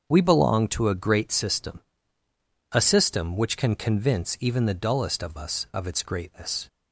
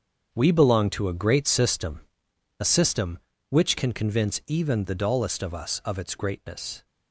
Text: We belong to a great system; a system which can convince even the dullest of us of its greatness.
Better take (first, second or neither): first